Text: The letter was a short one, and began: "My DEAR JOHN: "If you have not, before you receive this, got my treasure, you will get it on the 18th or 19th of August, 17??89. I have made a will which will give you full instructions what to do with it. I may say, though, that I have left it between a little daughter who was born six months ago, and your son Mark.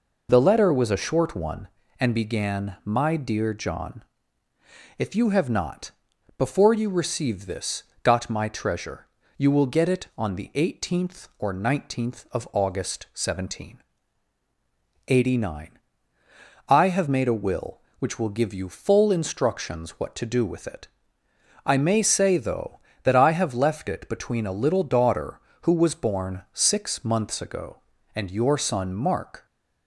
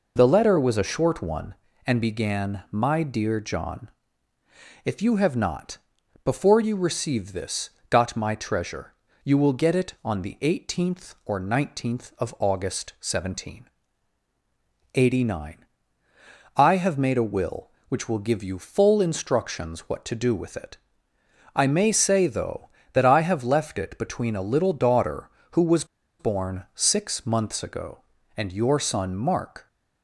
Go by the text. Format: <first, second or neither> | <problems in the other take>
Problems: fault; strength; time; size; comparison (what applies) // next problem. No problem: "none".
first | pauses between "was" and "born"; slight; at 25.8 s; 0.34 s long